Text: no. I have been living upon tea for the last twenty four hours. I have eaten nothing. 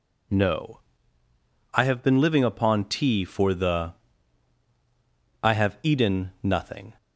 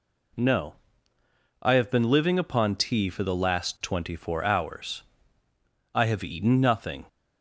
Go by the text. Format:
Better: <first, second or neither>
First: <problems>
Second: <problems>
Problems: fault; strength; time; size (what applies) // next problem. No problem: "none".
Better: second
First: skips "last twenty four hours"; at 4.6 s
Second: none